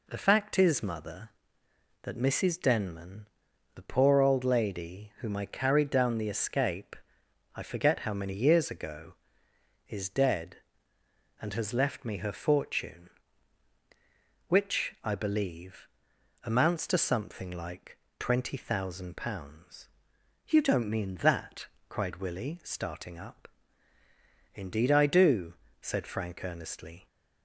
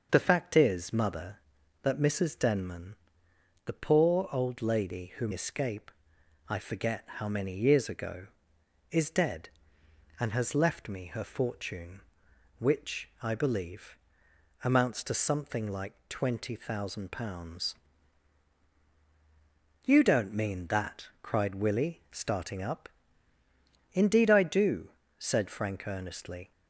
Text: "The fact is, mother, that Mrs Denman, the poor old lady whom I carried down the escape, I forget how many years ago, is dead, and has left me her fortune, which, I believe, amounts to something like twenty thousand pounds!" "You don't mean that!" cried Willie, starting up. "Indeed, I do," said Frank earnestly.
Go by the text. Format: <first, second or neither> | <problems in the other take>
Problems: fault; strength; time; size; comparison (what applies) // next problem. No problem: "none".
first | starts louder than the rest; until 1.1 s; 6.5 dB // skips "I carried down the"; at 5.3 s // pauses between "like" and "twenty"; slight; at 15.9 s; 0.16 s long; slight in the first